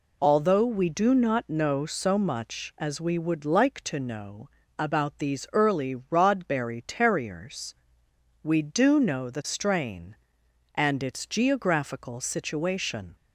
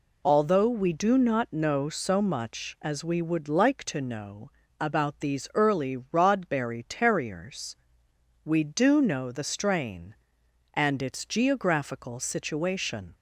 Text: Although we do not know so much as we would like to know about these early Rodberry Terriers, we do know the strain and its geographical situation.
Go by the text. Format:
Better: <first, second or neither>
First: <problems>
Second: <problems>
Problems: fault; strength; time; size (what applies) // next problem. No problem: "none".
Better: neither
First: pauses between "know" and "about"; slight; at 4.4 s; 0.30 s long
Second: pauses between "know" and "about"; slight; at 4.5 s; 0.30 s long